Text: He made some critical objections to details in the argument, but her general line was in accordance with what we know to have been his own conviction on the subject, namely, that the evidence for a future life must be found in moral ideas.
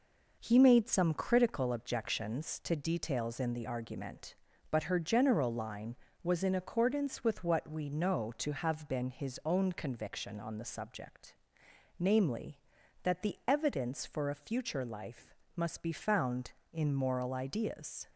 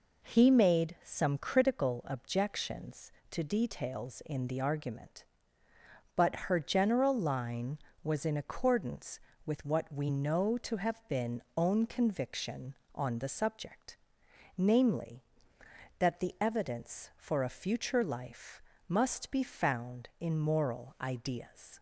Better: first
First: pauses between "life" and "must"; slight; at 15.3 s; 0.22 s long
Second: skips "his"; at 11.4 s // pauses between "life" and "must"; slight; at 18.6 s; 0.26 s long

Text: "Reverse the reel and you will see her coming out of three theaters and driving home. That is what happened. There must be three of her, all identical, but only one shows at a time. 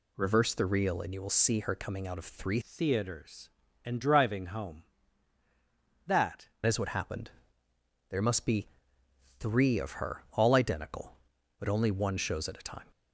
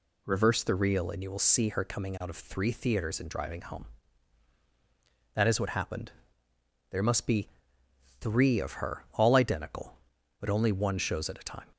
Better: second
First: changes voice from "theaters" to "That"; from 2.6 to 6.4 s; 3.8 s long // pauses between "be" and "three"; noticeable; at 8.6 s; 0.72 s long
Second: pauses between "be" and "three"; noticeable; at 7.4 s; 0.72 s long

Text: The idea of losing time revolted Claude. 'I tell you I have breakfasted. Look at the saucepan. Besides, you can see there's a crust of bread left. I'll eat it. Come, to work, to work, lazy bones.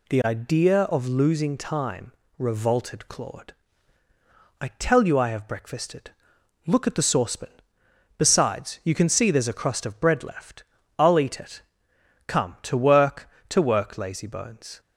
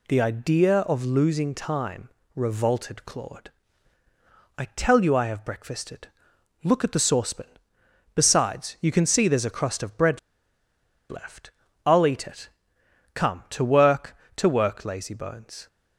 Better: first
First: pauses between "time" and "revolted"; slight; at 2.1 s; 0.26 s long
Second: pauses between "time" and "revolted"; slight; at 2.0 s; 0.26 s long // pauses between "bread" and "left"; noticeable; at 10.1 s; 0.91 s long

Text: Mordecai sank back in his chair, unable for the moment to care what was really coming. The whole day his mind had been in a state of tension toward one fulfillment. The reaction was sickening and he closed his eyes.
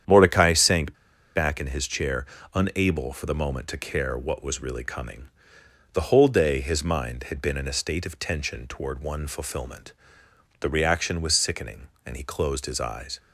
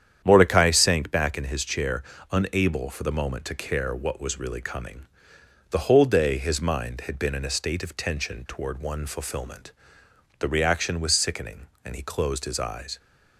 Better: second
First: starts louder than the rest; strong; until 1.4 s; 9 dB // pauses between "sank" and "back"; at 0.9 s; 0.42 s long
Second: starts louder than the rest; strong; until 1.2 s; 9 dB

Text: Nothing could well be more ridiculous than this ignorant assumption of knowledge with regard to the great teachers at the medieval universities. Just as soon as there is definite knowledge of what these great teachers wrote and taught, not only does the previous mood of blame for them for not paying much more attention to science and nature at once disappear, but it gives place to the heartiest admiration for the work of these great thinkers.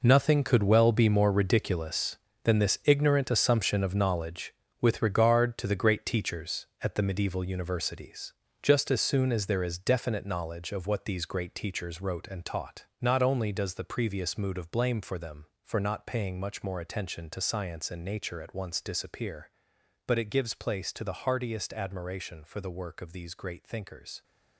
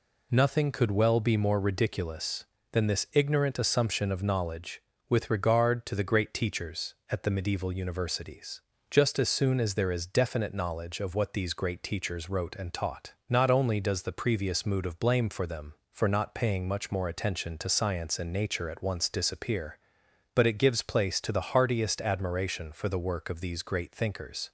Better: second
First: gets quieter; strong; throughout; 12 dB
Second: none

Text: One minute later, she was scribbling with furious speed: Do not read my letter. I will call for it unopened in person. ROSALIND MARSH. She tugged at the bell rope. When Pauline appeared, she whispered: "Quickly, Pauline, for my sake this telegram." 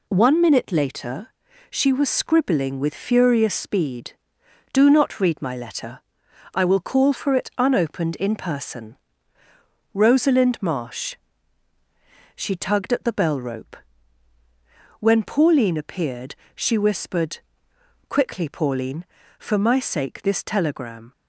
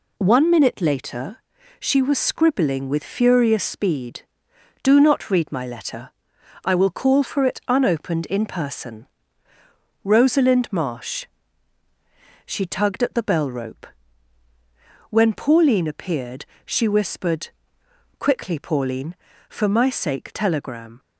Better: first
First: none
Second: skips "this"; at 20.3 s

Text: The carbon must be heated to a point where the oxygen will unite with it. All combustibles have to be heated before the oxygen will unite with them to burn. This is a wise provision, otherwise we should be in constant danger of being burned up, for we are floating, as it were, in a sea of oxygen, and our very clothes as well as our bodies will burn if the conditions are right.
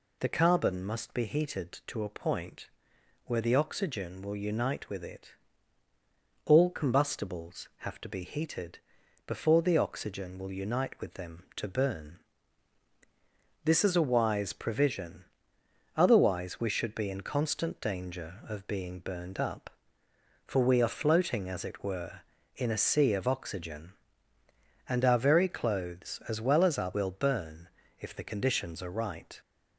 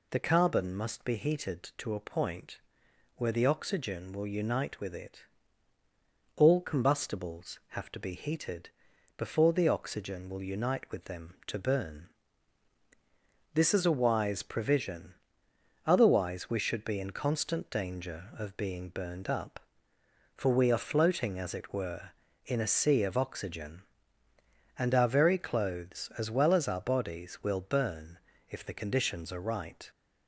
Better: second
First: pauses between "point" and "where"; noticeable; at 2.6 s; 0.58 s long // pauses between "heated" and "before"; noticeable; at 8.7 s; 0.48 s long // skips "bodies"; at 26.9 s // pauses between "burn" and "if"; slight; at 27.6 s; 0.30 s long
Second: pauses between "point" and "where"; noticeable; at 2.5 s; 0.58 s long // pauses between "heated" and "before"; noticeable; at 8.6 s; 0.48 s long // pauses between "burn" and "if"; slight; at 28.1 s; 0.30 s long

